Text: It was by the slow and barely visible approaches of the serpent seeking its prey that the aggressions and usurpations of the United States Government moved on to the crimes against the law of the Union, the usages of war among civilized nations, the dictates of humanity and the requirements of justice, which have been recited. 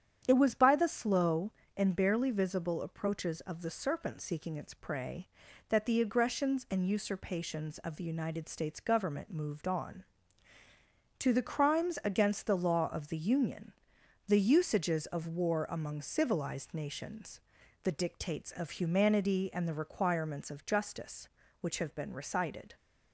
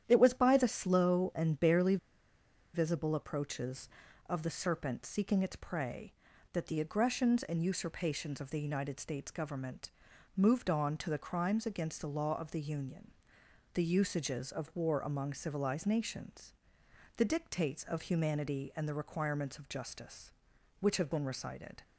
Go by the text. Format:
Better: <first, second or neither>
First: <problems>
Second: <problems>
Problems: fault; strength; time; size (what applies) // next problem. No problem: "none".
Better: first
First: starts louder than the rest; strong; until 1.2 s; 8.5 dB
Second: starts louder than the rest; strong; until 1.0 s; 10 dB // pauses between "barely" and "visible"; noticeable; at 1.9 s; 0.77 s long // pauses between "Government" and "moved"; noticeable; at 9.9 s; 0.46 s long